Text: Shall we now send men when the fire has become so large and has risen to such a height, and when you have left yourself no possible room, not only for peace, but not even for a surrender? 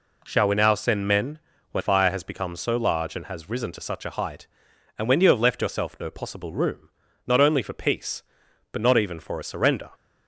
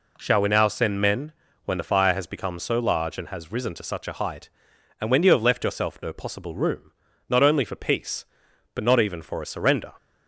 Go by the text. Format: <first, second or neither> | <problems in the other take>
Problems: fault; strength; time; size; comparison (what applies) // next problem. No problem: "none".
second | pauses between "men" and "when"; slight; at 1.3 s; 0.32 s long; slight in the second // skips "the"; at 1.8 s